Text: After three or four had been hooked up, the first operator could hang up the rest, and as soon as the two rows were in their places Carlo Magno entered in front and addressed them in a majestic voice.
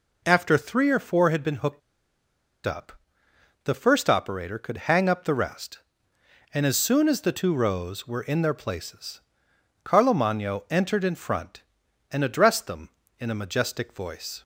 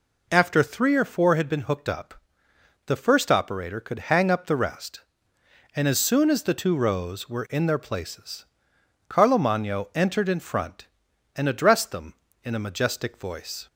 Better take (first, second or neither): second